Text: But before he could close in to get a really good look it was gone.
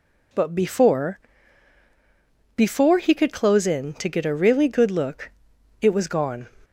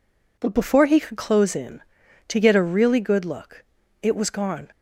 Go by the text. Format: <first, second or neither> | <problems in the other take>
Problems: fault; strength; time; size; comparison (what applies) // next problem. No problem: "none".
second | says "before" twice; at 2.5 s // pauses between "look" and "it"; noticeable; at 5.3 s; 0.50 s long; also in the second